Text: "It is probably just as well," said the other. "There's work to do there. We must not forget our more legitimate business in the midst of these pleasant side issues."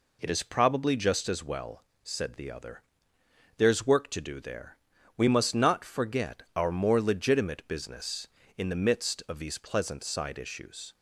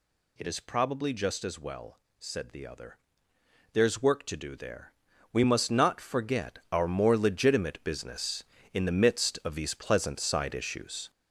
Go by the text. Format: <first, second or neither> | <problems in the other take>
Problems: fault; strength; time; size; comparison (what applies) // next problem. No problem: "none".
first | gets louder; strong; throughout; 7 dB